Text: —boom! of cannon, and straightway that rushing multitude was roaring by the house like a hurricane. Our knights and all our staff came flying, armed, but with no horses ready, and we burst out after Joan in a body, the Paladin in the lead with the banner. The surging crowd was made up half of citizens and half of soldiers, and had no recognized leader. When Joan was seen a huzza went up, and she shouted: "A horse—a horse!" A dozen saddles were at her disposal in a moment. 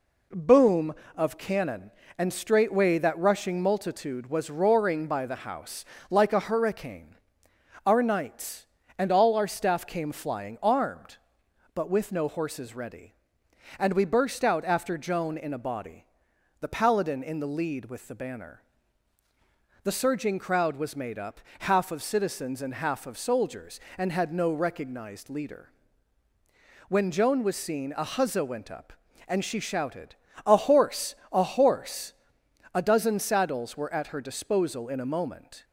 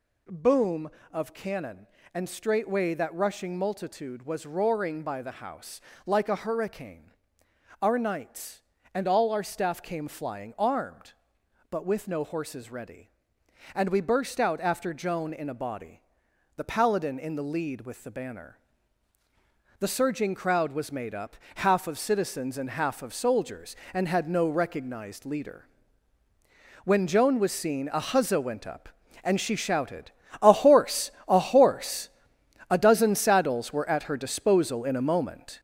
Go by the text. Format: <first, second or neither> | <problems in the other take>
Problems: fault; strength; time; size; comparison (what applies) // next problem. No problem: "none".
first | gets louder; strong; throughout; 7 dB // pauses between "house" and "like"; slight; at 5.7 s; 0.26 s long; slight in the first // pauses between "up" and "half"; slight; at 21.3 s; 0.20 s long; slight in the first